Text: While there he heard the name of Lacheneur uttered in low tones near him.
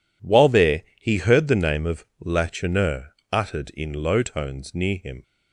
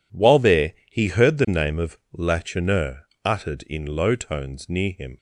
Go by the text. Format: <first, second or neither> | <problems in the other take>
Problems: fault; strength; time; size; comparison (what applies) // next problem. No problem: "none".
neither | pauses between "there" and "he"; slight; the same in both // pauses between "of" and "Lacheneur"; slight; the same in both // pauses between "Lacheneur" and "uttered"; slight; the same in both